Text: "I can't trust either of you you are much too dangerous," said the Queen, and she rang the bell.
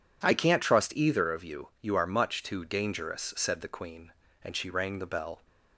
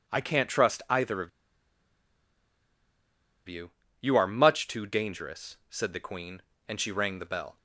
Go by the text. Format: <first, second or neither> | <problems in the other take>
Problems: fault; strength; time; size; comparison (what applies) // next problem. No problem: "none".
first | pauses between "of" and "you"; strong; at 1.2 s; 2.1 s long // pauses between "you" and "you"; slight; at 3.7 s; 0.28 s long